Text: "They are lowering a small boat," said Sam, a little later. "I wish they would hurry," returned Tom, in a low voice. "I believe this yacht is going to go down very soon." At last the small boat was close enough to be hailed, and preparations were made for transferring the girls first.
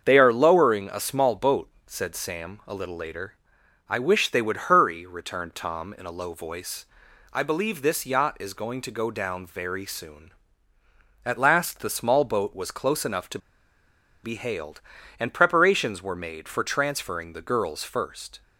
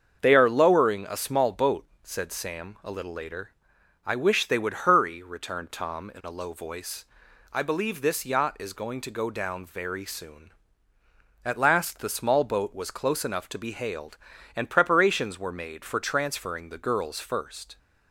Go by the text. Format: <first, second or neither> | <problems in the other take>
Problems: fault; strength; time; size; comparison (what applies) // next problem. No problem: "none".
second | starts louder than the rest; until 1.0 s; 7 dB; also in the second // pauses between "to" and "be"; noticeable; at 13.3 s; 0.85 s long